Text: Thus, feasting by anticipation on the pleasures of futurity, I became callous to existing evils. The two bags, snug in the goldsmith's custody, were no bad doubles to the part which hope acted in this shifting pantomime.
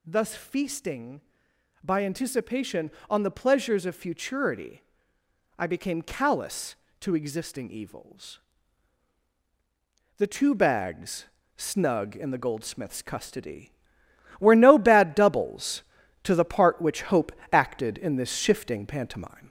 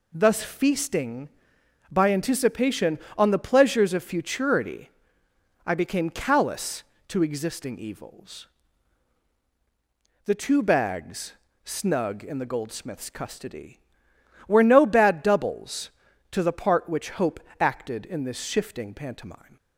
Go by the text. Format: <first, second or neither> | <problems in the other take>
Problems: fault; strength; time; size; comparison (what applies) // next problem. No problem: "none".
second | gets louder; slight; throughout; 3 dB // pauses between "hope" and "acted"; slight; at 17.3 s; 0.20 s long; slight in the second